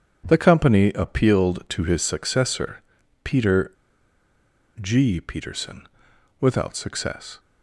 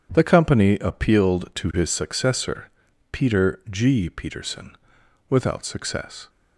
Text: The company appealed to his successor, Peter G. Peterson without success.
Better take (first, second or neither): second